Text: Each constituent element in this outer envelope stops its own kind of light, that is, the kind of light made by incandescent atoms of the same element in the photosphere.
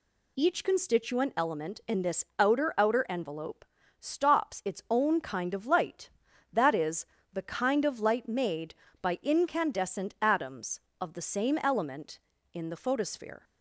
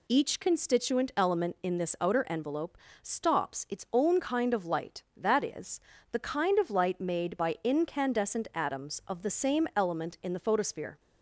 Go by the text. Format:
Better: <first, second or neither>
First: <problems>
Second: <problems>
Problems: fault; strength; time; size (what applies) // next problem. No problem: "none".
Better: second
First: says "outer" twice; at 2.7 s // pauses between "envelope" and "stops"; at 3.6 s; 0.38 s long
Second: pauses between "envelope" and "stops"; slight; at 2.7 s; 0.24 s long